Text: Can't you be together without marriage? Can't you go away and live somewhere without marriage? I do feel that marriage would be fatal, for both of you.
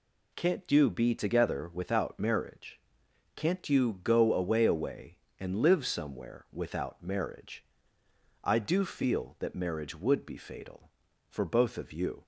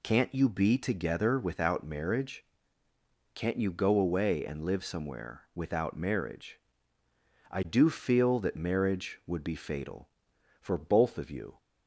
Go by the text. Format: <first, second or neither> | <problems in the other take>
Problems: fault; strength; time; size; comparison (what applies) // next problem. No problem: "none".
second | says "away" twice; at 4.6 s